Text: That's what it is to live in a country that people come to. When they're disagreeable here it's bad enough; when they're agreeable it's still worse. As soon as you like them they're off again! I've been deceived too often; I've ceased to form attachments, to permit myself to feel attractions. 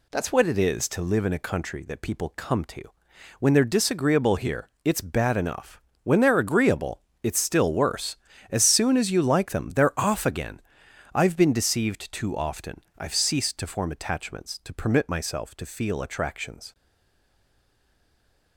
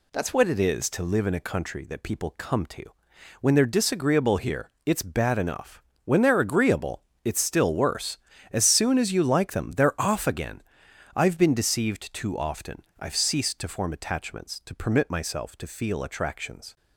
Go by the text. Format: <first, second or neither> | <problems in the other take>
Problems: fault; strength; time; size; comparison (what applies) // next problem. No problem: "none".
second | pauses between "agreeable" and "it's"; slight; at 7.0 s; 0.20 s long; slight in the second // stays silent after the last word; noticeable; from 16.7 s on; 1.8 s long